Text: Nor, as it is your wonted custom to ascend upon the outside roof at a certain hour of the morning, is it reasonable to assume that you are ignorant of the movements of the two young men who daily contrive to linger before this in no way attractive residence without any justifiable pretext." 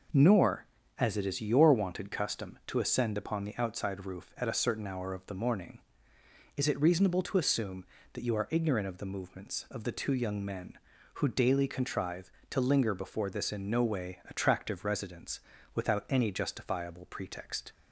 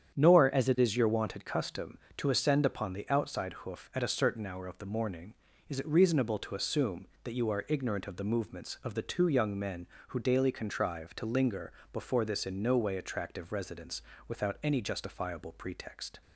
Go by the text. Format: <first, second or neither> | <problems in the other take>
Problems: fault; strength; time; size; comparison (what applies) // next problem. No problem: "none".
first | starts louder than the rest; strong; until 1.1 s; 8.5 dB // says "hoof" for "roof"; at 3.6 s // pauses between "linger" and "before"; slight; at 11.7 s; 0.18 s long // pauses between "residence" and "without"; slight; at 14.0 s; 0.26 s long; slight in the first